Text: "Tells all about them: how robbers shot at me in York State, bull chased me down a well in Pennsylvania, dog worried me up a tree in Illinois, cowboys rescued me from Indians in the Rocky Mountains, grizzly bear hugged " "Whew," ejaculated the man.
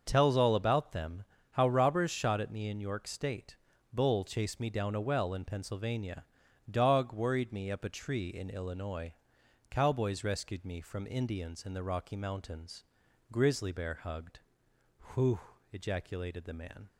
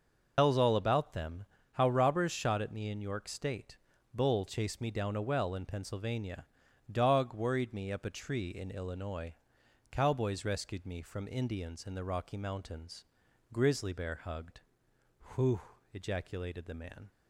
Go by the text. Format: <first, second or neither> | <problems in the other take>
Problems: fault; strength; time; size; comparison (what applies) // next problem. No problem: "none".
first | loses the start of "Tells"; at 0.3 s; 115 ms // starts louder than the rest; noticeable; until 1.3 s; 6 dB; also in the first